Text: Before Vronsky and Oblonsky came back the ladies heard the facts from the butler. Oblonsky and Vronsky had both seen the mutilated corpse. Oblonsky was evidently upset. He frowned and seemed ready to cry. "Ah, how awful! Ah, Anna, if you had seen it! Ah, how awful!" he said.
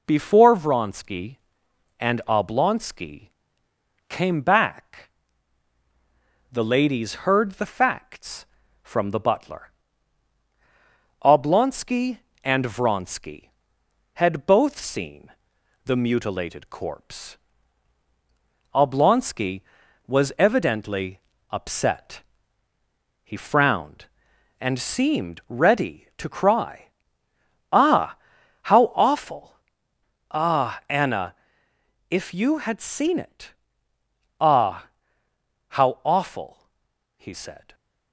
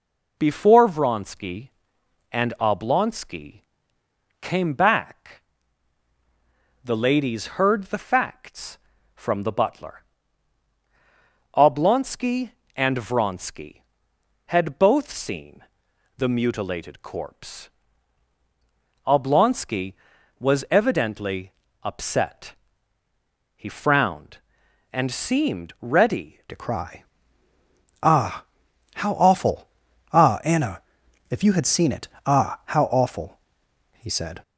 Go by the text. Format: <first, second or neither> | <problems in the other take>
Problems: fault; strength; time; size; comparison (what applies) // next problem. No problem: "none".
first | pauses between "Oblonsky" and "came"; noticeable; at 3.6 s; 0.78 s long; noticeable in the first // pauses between "back" and "the"; strong; at 5.4 s; 1.4 s long; strong in the first // pauses between "seen" and "the"; noticeable; at 15.6 s; 0.54 s long; noticeable in the first // pauses between "evidently" and "upset"; slight; at 21.5 s; 0.32 s long; slight in the first // changes voice at "to"; from 26.4 s on; 8.0 s long